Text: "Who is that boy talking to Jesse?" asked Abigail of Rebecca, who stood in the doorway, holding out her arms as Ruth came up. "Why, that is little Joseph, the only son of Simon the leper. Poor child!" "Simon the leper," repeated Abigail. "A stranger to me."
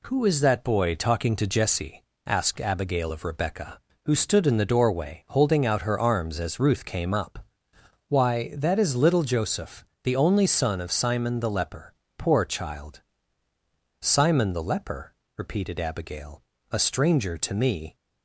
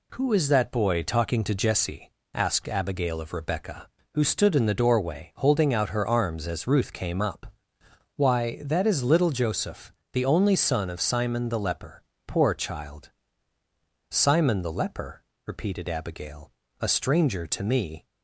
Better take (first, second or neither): neither